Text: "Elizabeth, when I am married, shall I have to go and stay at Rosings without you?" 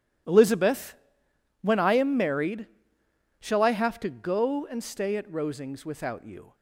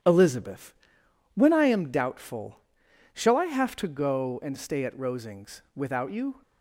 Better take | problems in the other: first | starts louder than the rest; strong; until 1.6 s; 10.5 dB // says "doubtful" for "married"; at 1.9 s

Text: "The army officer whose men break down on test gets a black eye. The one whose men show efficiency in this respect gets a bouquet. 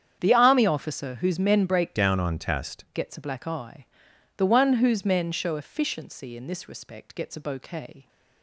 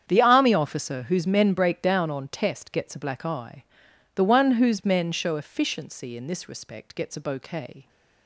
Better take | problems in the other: second | starts louder than the rest; strong; until 1.2 s; 8.5 dB; strong in the second // changes voice from "down" to "test"; from 1.9 to 2.8 s; 0.9 s long

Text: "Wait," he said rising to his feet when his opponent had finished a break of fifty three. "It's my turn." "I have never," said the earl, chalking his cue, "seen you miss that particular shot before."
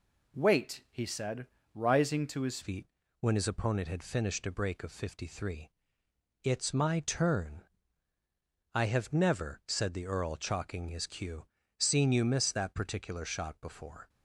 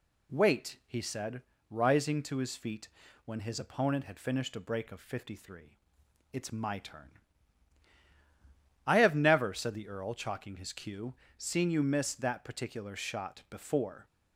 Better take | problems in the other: second | pauses between "said" and "rising"; slight; at 1.4 s; 0.30 s long; slight in the second // changes voice at "feet"; from 2.6 s on; 11.4 s long // pauses between "feet" and "when"; slight; at 2.8 s; 0.34 s long; also in the second

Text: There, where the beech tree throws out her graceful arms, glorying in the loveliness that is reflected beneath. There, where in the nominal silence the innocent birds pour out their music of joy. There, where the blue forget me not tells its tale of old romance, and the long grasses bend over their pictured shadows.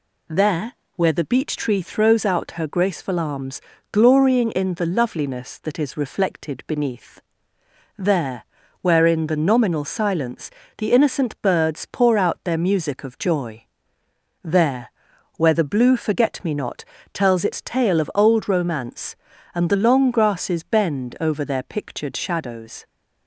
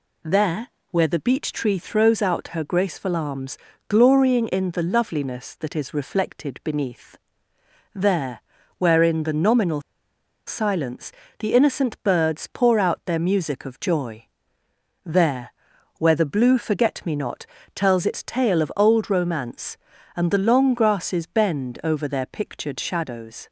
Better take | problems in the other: first | pauses between "nominal" and "silence"; noticeable; at 9.8 s; 0.65 s long // pauses between "silence" and "the"; slight; at 11.1 s; 0.28 s long; slight in the first // pauses between "not" and "tells"; slight; at 17.4 s; 0.30 s long; slight in the first

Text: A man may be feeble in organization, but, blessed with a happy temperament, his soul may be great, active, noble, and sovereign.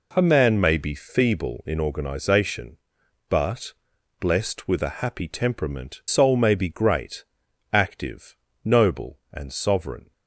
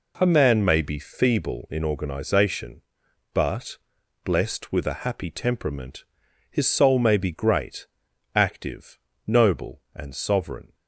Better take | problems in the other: second | skips "his"; at 6.0 s

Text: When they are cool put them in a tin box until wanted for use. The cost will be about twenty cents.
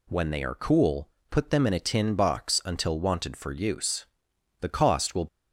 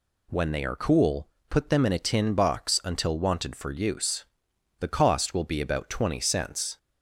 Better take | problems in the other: second | pauses between "cool" and "put"; slight; at 1.0 s; 0.22 s long; slight in the second // stops before "be about twenty cents"; at 5.2 s

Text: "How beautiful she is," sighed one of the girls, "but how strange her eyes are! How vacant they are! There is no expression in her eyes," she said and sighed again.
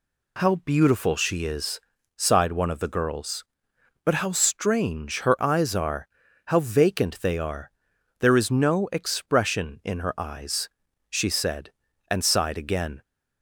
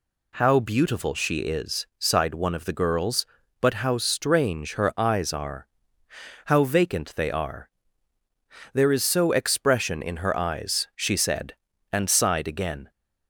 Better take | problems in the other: first | says "so" for "no"; at 9.0 s

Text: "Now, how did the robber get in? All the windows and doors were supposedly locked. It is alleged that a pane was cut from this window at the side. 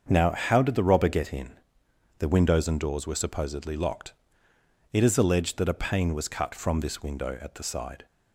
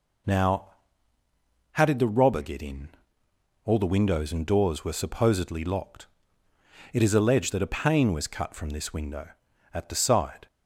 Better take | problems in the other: second | starts louder than the rest; until 1.0 s; 7 dB // skips "All"; at 1.8 s

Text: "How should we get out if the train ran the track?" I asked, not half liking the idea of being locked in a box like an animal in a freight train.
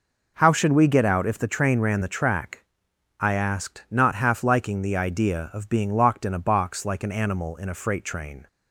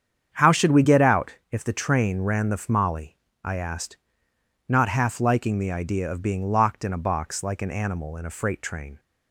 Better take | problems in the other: first | starts louder than the rest; strong; until 1.3 s; 8 dB // pauses between "out" and "if"; slight; at 1.3 s; 0.16 s long // says "fmali" for "track"; at 2.5 s

